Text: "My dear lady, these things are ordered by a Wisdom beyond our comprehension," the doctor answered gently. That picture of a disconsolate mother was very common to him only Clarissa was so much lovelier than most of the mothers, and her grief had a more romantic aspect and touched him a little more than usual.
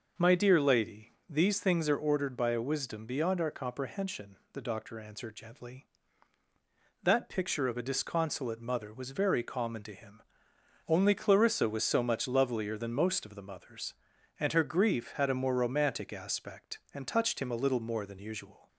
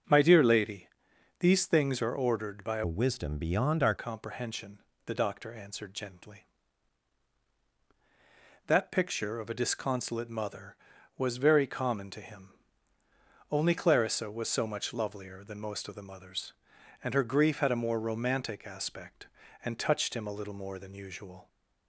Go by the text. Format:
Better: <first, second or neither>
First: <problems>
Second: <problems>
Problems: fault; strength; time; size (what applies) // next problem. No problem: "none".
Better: first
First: pauses between "him" and "only"; noticeable; at 10.2 s; 0.64 s long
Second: starts louder than the rest; strong; until 1.5 s; 7.5 dB // changes voice from "Wisdom" to "our"; from 2.8 to 3.9 s; 1.1 s long // pauses between "him" and "only"; at 12.4 s; 1.0 s long